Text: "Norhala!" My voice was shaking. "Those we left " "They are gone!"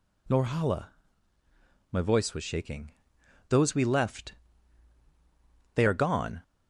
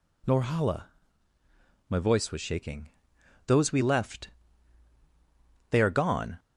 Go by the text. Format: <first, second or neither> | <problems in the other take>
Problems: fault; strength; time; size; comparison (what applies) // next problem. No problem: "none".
neither | none